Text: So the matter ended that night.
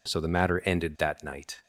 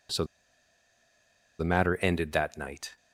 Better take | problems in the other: first | pauses between "So" and "the"; strong; at 0.2 s; 1.3 s long

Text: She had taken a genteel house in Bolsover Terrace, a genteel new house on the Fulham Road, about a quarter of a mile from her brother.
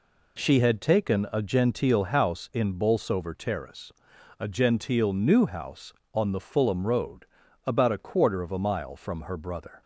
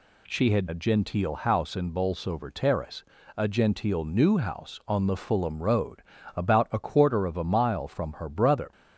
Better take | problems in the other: first | skips "taken"; at 0.6 s

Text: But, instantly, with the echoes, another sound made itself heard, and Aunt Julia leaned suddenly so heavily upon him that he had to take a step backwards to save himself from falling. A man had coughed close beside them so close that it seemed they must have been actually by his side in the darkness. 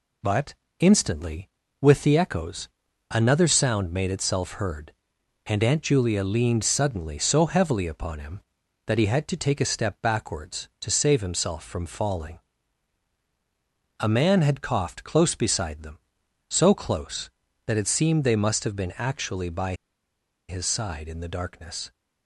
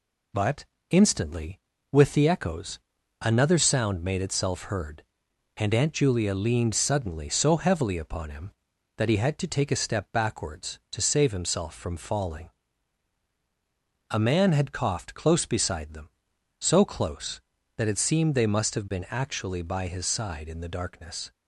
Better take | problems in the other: second | pauses between "by" and "his"; noticeable; at 19.7 s; 0.75 s long

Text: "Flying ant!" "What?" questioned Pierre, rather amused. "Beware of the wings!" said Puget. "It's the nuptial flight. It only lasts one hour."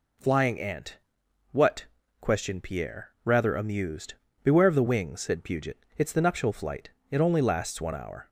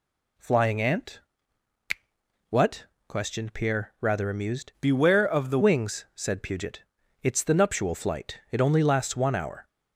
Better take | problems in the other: first | changes voice from "Beware" to "the"; from 4.7 to 5.5 s; 0.8 s long

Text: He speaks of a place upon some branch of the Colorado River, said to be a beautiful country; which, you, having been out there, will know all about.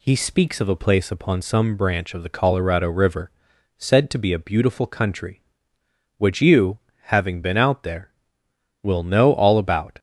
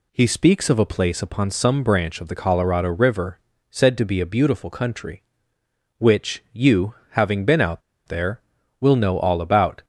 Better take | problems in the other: first | pauses between "out" and "there"; slight; at 7.8 s; 0.26 s long

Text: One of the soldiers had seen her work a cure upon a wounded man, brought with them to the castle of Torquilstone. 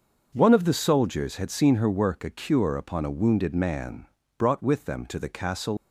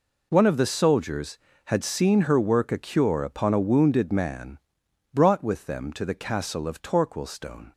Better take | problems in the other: second | starts louder than the rest; until 1.3 s; 6 dB // stops before "of Torquilstone"; at 5.7 s

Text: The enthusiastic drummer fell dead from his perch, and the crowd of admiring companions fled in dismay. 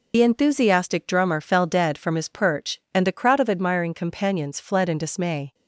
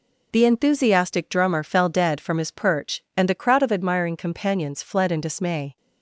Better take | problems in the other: second | loses the start of "The"; at 0.1 s; 45 ms

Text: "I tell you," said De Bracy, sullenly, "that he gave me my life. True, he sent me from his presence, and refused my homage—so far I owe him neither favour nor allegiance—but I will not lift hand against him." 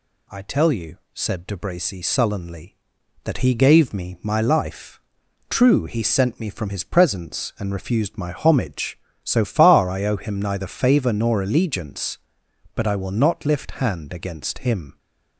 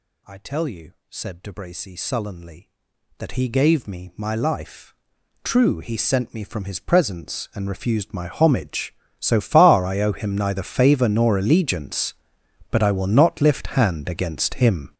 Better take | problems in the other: first | gets louder; strong; throughout; 11.5 dB

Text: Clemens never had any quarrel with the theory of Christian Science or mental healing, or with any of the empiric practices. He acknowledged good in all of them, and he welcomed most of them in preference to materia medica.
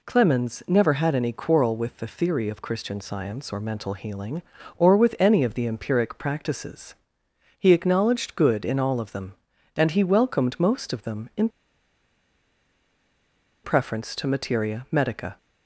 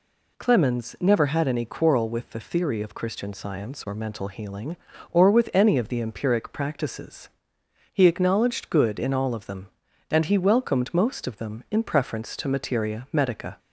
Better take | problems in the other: second | pauses between "in" and "preference"; strong; at 11.4 s; 2.1 s long

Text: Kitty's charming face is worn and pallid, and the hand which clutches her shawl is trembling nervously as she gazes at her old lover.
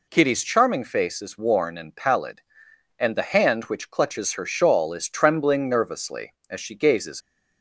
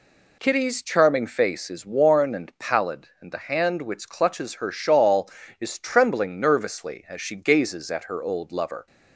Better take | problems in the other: second | stops before "at her old lover"; at 7.2 s

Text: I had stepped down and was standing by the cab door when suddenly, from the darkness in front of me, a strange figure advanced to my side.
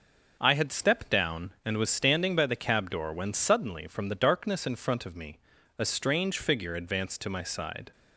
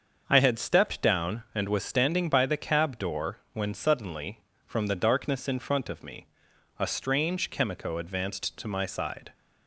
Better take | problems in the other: first | starts louder than the rest; until 1.2 s; 7 dB // pauses between "door" and "when"; slight; at 3.3 s; 0.16 s long // says "chemico" for "figure"; at 7.5 s

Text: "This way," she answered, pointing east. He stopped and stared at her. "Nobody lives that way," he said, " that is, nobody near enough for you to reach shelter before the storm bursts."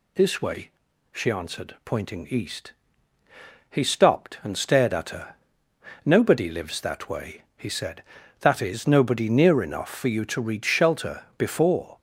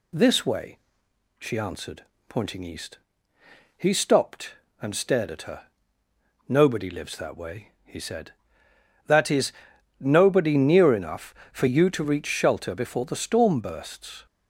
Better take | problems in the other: second | stops before "the storm bursts"; at 11.9 s

